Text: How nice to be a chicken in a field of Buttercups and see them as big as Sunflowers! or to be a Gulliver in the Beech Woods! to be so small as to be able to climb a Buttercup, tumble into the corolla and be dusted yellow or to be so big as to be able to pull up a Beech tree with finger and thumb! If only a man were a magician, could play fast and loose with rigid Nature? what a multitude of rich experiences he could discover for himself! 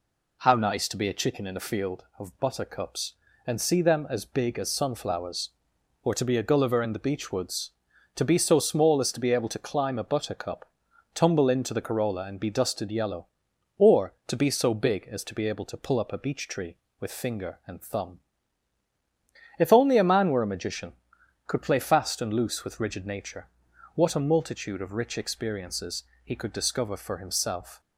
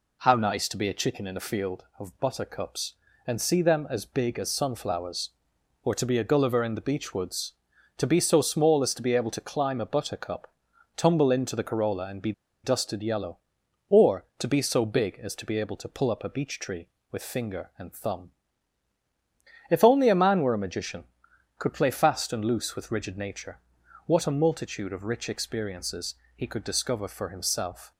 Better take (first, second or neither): first